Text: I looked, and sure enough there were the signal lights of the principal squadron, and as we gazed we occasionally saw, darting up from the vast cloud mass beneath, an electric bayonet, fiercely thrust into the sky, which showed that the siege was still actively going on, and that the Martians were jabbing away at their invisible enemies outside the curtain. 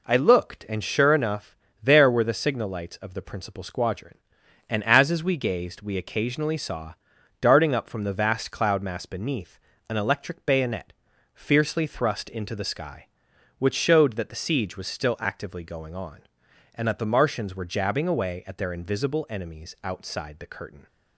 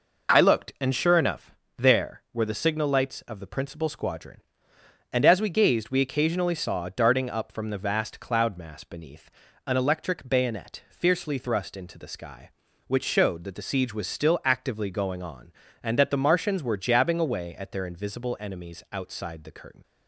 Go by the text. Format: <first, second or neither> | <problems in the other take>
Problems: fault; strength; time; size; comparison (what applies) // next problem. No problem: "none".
second | pauses between "enough" and "there"; slight; at 1.5 s; 0.26 s long; slight in the second // says "as" twice; at 5.1 s